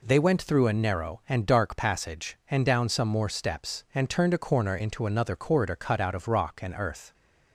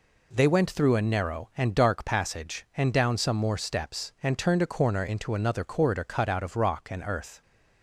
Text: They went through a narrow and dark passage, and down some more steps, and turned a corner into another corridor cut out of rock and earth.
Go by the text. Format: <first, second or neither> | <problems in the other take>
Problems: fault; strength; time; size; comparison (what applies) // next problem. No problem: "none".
neither | none